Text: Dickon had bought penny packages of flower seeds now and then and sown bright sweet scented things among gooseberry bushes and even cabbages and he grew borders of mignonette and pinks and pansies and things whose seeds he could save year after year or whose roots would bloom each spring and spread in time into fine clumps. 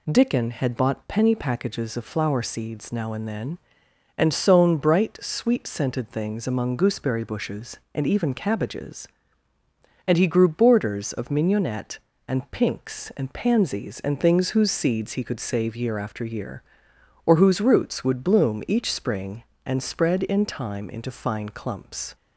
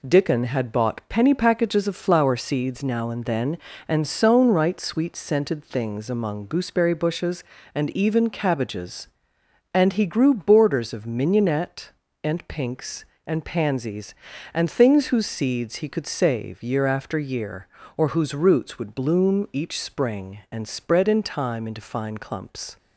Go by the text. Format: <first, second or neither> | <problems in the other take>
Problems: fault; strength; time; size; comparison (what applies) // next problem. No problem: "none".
first | says "right" for "bright"; at 4.4 s